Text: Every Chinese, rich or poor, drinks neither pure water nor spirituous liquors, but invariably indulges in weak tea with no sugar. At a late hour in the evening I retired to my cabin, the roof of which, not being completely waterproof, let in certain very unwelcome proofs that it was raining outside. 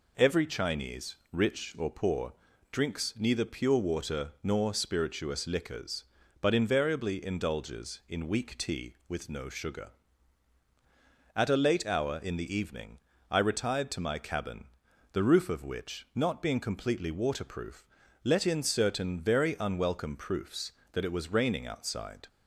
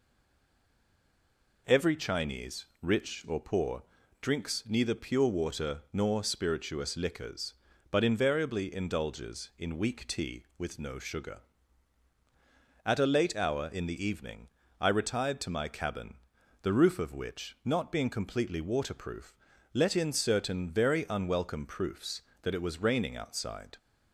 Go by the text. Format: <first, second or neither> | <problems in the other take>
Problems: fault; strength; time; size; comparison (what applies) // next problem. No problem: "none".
first | stays silent before the first word; noticeable; until 1.6 s; 1.6 s long // pauses between "evening" and "I"; slight; at 14.4 s; 0.32 s long; slight in the first